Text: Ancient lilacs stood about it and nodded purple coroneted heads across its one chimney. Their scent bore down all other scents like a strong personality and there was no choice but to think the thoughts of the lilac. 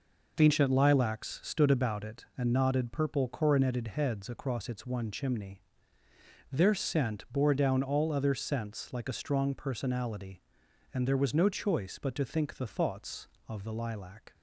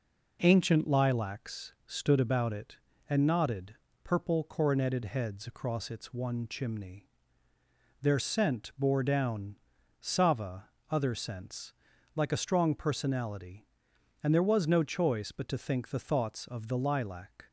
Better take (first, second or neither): first